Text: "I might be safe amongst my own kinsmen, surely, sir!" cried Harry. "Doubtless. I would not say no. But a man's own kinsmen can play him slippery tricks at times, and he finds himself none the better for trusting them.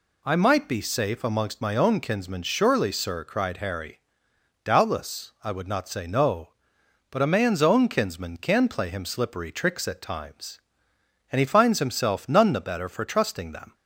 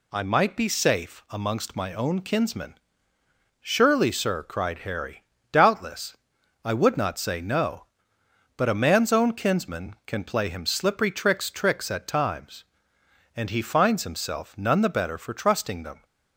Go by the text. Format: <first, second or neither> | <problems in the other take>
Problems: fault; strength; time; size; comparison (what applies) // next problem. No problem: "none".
first | says "tricks" twice; at 11.5 s